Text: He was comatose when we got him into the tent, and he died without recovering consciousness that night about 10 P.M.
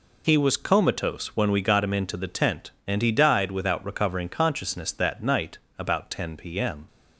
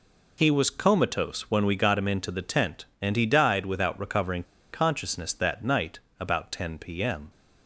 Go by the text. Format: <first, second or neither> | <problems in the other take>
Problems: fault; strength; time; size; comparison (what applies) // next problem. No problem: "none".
first | pauses between "recovering" and "consciousness"; slight; at 4.4 s; 0.27 s long // pauses between "night" and "about"; slight; at 5.9 s; 0.20 s long; slight in the first